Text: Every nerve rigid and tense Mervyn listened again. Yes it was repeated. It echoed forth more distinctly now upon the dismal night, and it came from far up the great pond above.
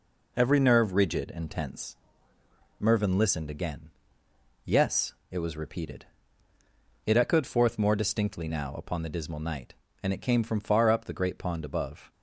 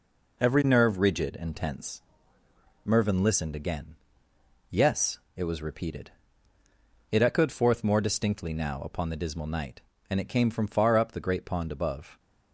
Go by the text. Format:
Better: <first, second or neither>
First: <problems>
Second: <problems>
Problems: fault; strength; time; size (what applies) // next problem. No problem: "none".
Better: neither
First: pauses between "tense" and "Mervyn"; noticeable; at 1.9 s; 0.84 s long // pauses between "Yes" and "it"; slight; at 5.1 s; 0.16 s long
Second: pauses between "tense" and "Mervyn"; noticeable; at 2.0 s; 0.84 s long // pauses between "Yes" and "it"; slight; at 5.1 s; 0.16 s long